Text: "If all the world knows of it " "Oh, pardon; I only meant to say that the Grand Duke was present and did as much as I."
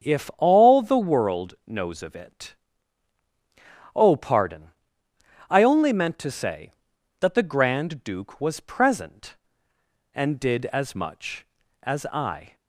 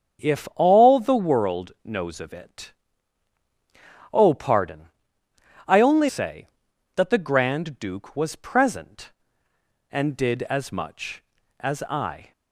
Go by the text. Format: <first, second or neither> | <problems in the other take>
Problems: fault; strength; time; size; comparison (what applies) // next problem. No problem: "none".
first | starts louder than the rest; noticeable; until 1.2 s; 6 dB; noticeable in the first // skips "meant to"; at 6.0 s